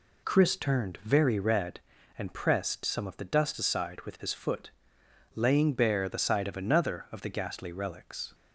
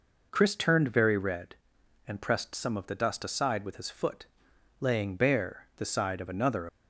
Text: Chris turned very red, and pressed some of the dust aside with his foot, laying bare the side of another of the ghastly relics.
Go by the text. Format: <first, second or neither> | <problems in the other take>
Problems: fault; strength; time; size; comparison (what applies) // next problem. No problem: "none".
first | stops before "of the ghastly relics"; at 6.6 s